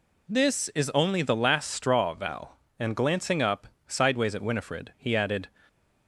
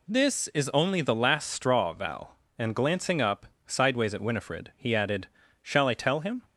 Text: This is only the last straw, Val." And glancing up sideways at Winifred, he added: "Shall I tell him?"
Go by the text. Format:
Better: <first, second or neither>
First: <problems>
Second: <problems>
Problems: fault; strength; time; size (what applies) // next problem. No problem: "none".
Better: second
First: pauses between "up" and "sideways"; slight; at 3.6 s; 0.20 s long // stops before "Shall I tell him"; at 5.6 s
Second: pauses between "up" and "sideways"; slight; at 3.4 s; 0.20 s long